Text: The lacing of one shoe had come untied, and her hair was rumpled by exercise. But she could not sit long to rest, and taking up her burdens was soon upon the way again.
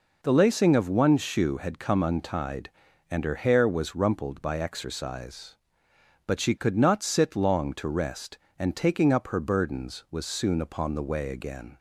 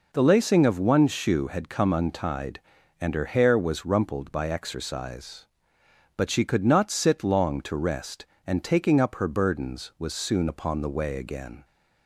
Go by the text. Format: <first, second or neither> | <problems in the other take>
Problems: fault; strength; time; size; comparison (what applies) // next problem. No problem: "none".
neither | none